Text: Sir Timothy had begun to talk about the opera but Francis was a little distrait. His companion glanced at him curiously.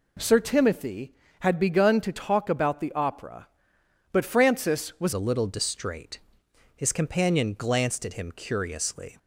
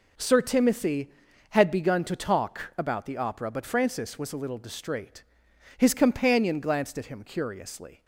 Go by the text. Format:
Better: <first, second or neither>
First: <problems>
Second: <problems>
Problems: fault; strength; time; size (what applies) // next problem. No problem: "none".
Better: second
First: changes voice at "a"; from 5.1 s on; 4.0 s long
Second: none